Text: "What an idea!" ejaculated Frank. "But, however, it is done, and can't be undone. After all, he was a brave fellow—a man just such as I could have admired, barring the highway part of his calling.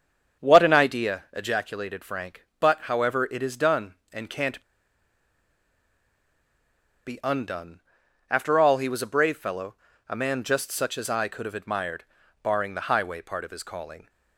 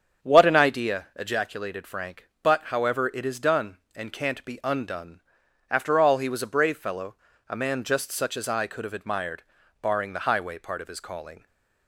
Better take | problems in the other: second | starts louder than the rest; strong; until 1.4 s; 7.5 dB; strong in the second // pauses between "can't" and "be"; strong; at 4.6 s; 2.4 s long

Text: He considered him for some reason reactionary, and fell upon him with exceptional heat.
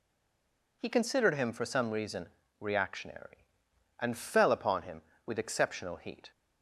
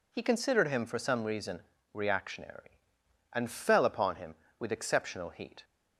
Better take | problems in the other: second | stays silent before the first word; slight; until 0.8 s; 0.8 s long // pauses between "reason" and "reactionary"; slight; at 2.2 s; 0.32 s long; slight in the second

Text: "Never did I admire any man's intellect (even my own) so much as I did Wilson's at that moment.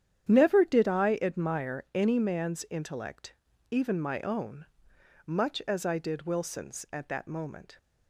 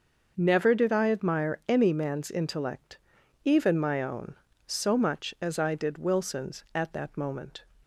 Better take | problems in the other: second | starts louder than the rest; strong; until 1.3 s; 9.5 dB; noticeable in the second // skips "so"; at 4.9 s

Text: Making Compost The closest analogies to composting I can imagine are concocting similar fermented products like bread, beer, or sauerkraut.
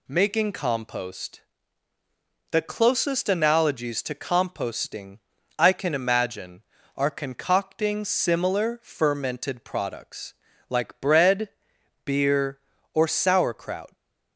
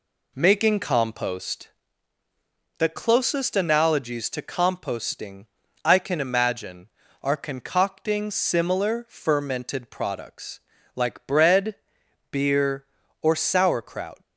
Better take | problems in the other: first | starts louder than the rest; slight; until 2.0 s; 2.5 dB // pauses between "Compost" and "The"; at 1.6 s; 1.1 s long; also in the first // pauses between "composting" and "I"; at 5.4 s; 0.38 s long; also in the first // pauses between "products" and "like"; slight; at 10.5 s; 0.36 s long; slight in the first

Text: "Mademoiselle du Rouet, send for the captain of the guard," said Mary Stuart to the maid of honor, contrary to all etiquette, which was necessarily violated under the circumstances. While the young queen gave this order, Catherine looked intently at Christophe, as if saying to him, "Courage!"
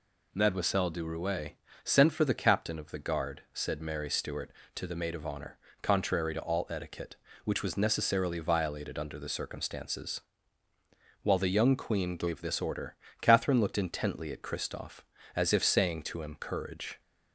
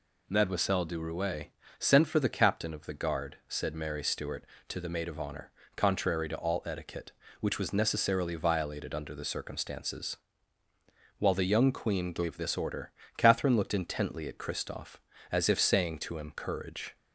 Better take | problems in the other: neither | none

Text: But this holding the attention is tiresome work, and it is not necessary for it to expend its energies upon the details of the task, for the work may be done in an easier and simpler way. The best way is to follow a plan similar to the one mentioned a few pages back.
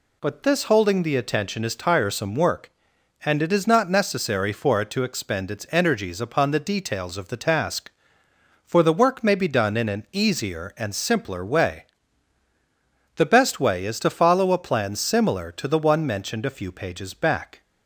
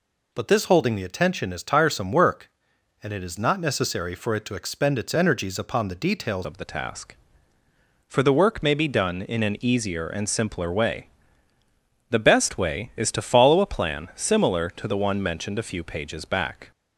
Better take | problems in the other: first | changes voice at "of"; from 6.4 s on; 10.3 s long

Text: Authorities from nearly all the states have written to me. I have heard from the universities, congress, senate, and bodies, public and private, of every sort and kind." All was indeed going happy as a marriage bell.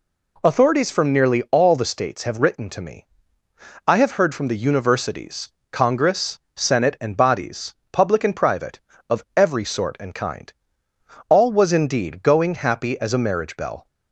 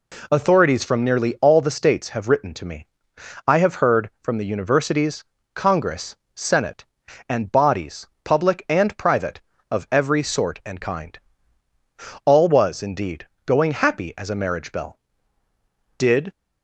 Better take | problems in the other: first | pauses between "indeed" and "going"; slight; at 13.2 s; 0.20 s long // goes on to say "Did"; slight; from 15.9 s on; 0.34 s long

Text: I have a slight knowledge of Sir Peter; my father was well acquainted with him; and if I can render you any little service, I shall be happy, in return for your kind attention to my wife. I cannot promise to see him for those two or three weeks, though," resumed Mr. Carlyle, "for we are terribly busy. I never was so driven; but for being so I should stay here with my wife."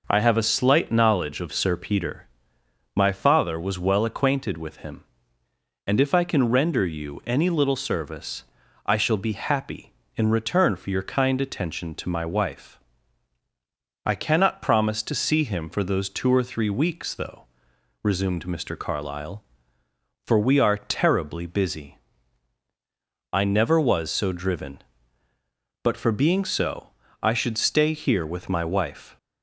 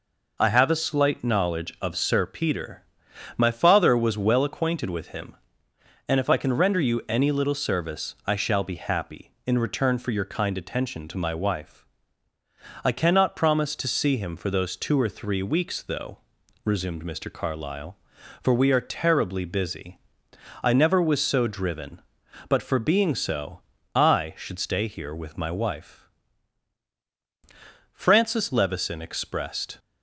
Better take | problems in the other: first | pauses between "so" and "I"; slight; at 23.6 s; 0.32 s long; slight in the first // goes on to say "Francis Levison expressed"; strong; from 27.9 s on; 1.8 s long

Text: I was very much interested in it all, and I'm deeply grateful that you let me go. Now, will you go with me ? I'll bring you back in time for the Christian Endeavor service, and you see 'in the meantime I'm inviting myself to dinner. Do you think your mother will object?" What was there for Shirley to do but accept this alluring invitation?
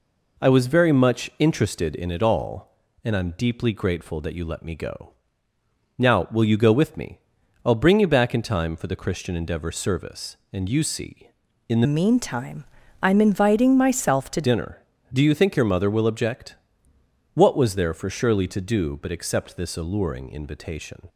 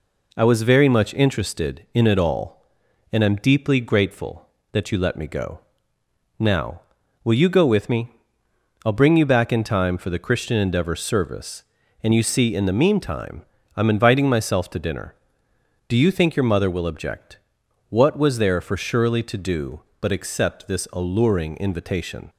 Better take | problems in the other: second | changes voice from "meantime" to "to"; from 11.8 to 14.4 s; 2.6 s long // pauses between "meantime" and "I'm"; at 12.6 s; 0.38 s long; slight in the second

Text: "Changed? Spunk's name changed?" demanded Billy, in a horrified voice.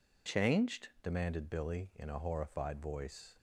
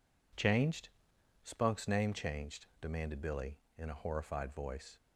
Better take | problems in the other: second | skips "Spunk's name changed"; at 0.9 s

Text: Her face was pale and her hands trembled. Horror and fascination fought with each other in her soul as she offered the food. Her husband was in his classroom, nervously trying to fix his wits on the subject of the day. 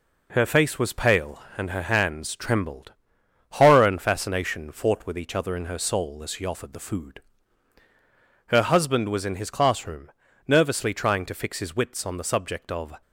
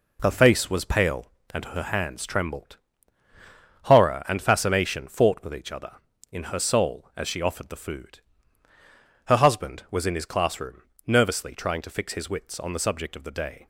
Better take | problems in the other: second | stops before "the day"; at 13.0 s

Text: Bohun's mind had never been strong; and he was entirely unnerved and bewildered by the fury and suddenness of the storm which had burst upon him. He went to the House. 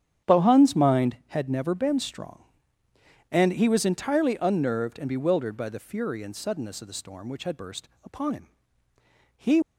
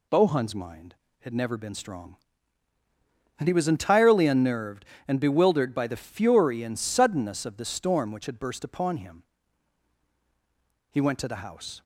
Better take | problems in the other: second | starts louder than the rest; strong; until 1.3 s; 9.5 dB // pauses between "burst" and "upon"; slight; at 7.8 s; 0.16 s long // stops before "went to the House"; at 9.6 s

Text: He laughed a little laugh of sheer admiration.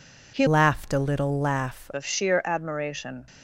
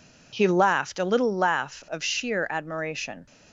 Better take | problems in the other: second | changes voice from "laughed" to "laugh"; from 0.4 to 1.8 s; 1.4 s long

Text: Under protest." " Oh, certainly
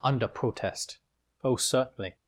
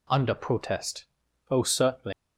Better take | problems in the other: first | leaves "certainly" unfinished; at 2.1 s; 95 ms

